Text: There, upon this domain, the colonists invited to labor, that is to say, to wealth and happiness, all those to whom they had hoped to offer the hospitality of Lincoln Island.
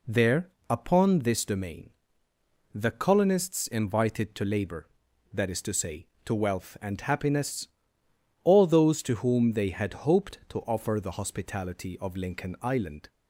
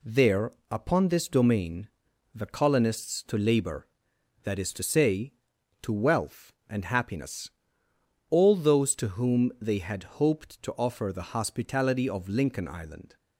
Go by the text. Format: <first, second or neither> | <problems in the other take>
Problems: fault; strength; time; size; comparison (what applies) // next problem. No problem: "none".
first | skips "invited"; at 3.2 s